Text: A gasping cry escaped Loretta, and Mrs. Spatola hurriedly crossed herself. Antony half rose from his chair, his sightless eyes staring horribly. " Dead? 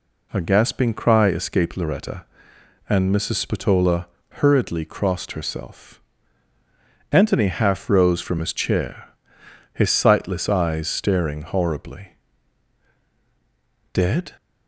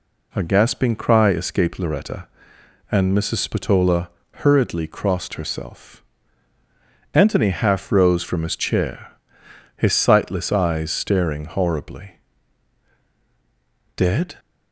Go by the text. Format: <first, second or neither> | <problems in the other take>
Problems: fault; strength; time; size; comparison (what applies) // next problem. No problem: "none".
neither | pauses between "Spatola" and "hurriedly"; slight; the same in both